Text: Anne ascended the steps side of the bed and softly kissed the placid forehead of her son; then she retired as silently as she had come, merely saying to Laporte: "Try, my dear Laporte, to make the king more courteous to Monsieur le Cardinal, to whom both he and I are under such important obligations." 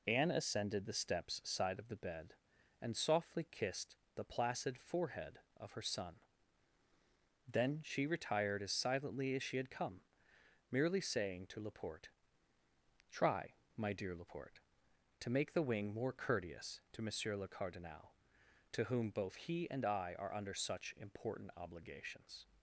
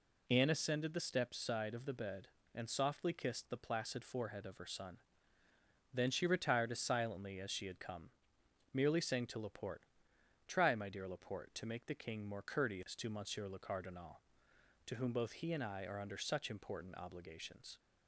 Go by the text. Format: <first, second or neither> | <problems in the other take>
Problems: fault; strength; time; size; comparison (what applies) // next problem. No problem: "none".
second | pauses between "kissed" and "the"; slight; at 3.9 s; 0.22 s long // says "wing" for "king"; at 15.6 s